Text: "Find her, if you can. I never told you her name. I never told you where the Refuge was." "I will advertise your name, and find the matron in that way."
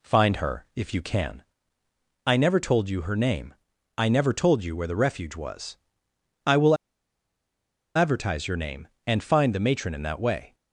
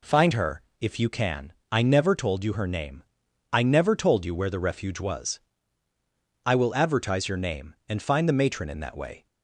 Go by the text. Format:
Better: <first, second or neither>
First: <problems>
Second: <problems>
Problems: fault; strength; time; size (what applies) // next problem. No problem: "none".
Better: second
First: pauses between "will" and "advertise"; at 6.7 s; 1.2 s long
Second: none